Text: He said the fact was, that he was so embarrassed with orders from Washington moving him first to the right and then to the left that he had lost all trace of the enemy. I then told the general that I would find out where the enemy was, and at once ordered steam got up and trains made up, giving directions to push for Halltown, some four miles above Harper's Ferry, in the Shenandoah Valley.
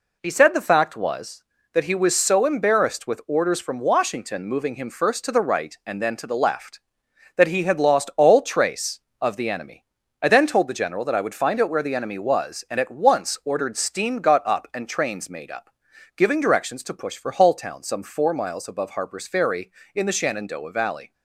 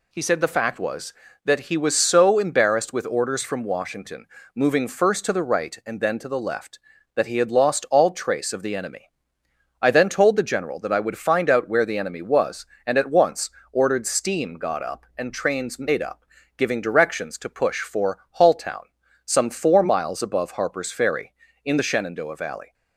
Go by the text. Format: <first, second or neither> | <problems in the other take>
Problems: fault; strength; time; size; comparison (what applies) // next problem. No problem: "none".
first | pauses between "Washington" and "moving"; slight; at 4.2 s; 0.28 s long // skips "him"; at 4.8 s // pauses between "once" and "ordered"; slight; at 13.4 s; 0.24 s long // pauses between "for" and "Halltown"; slight; at 18.1 s; 0.20 s long